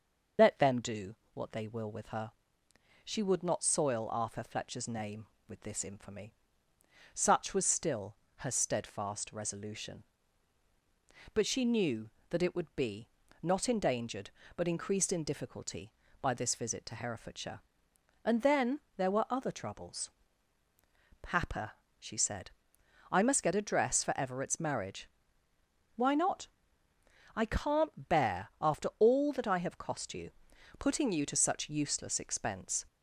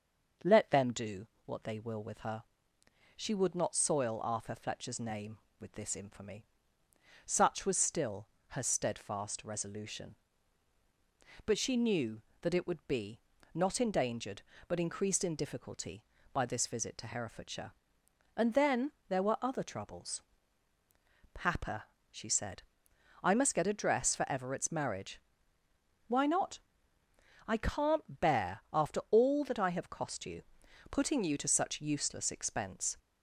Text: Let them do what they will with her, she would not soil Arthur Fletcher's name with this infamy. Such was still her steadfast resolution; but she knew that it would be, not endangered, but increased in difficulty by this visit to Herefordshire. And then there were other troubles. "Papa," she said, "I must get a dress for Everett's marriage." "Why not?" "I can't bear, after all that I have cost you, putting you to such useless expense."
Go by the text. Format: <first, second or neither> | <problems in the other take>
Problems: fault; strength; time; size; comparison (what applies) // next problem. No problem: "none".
second | loses the start of "Let"; at 0.3 s; 95 ms // starts louder than the rest; until 1.5 s; 6 dB; also in the second // pauses between "do" and "what"; slight; at 1.1 s; 0.18 s long; slight in the second // pauses between "still" and "her"; slight; at 8.1 s; 0.22 s long; slight in the second // pauses between "then" and "there"; slight; at 18.7 s; 0.18 s long; slight in the second